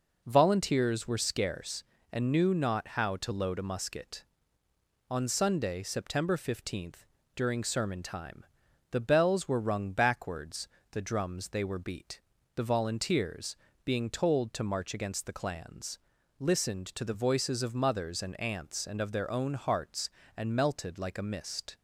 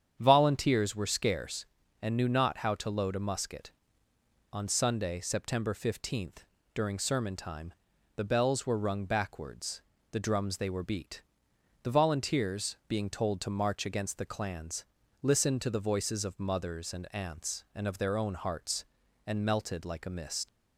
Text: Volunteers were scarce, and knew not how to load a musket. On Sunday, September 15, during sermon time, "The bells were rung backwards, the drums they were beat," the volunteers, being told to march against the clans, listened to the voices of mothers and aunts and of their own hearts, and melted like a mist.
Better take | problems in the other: first | starts louder than the rest; strong; until 1.2 s; 8 dB // leaves "mist" unfinished; at 20.4 s; 70 ms

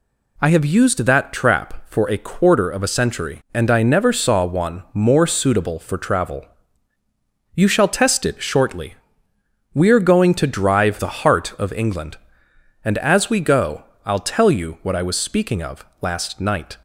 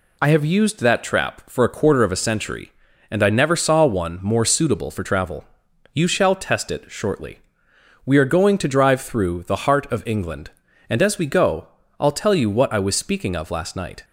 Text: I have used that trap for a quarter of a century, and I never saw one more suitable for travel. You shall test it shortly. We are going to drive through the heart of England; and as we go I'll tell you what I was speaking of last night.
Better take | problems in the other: second | skips "through"; at 10.9 s // pauses between "go" and "I'll"; slight; at 13.8 s; 0.22 s long; slight in the second // pauses between "of" and "last"; slight; at 15.8 s; 0.16 s long

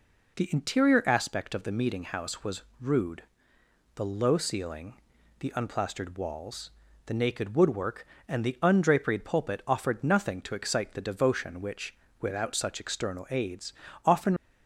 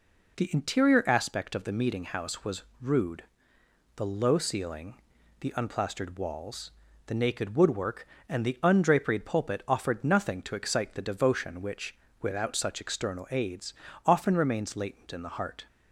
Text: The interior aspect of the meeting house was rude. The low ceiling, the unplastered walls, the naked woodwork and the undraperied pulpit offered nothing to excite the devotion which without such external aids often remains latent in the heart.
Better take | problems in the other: second | pauses between "was" and "rude"; slight; at 2.6 s; 0.18 s long; slight in the second // pauses between "which" and "without"; slight; at 11.9 s; 0.26 s long; slight in the second // pauses between "aids" and "often"; slight; at 13.7 s; 0.32 s long; slight in the second // stops before "remains latent in the heart"; at 14.3 s

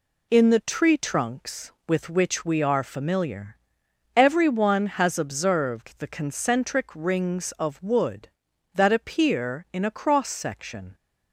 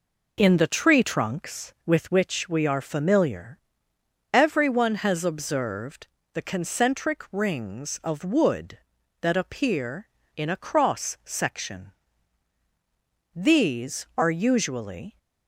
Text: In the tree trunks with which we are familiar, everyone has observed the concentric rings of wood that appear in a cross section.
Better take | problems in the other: first | pauses between "observed" and "the"; slight; at 6.0 s; 0.28 s long // goes on to say "These are usually"; strong; from 13.3 s on; 1.8 s long

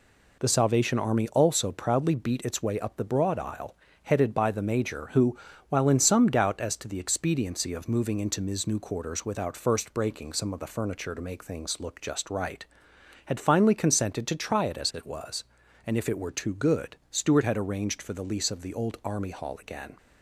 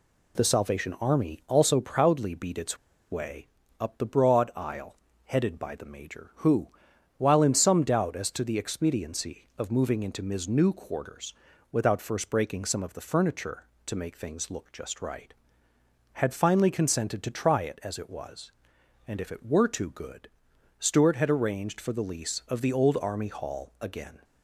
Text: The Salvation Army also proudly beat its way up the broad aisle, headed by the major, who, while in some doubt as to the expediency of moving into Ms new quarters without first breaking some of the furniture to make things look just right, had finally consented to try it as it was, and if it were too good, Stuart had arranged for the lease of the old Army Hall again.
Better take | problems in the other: first | pauses between "its" and "way"; slight; at 2.7 s; 0.34 s long // pauses between "way" and "up"; slight; at 3.4 s; 0.32 s long // pauses between "quarters" and "without"; at 11.3 s; 0.38 s long

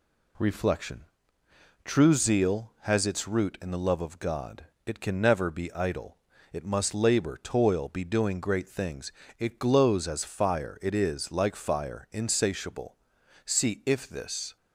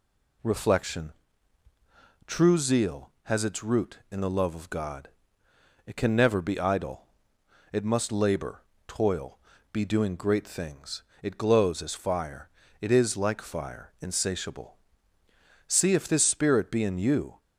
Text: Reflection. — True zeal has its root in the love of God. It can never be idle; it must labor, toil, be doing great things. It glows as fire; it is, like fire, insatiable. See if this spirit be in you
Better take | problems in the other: second | stops before "spirit be in you"; at 14.5 s

